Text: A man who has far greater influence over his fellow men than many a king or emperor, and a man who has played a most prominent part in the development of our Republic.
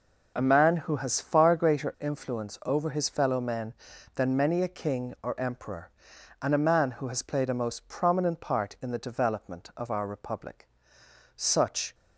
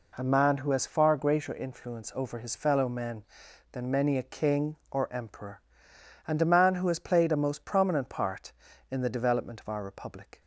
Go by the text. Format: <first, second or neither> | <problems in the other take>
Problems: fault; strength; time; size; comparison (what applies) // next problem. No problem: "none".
second | goes on to say "Such"; from 11.3 s on; 0.58 s long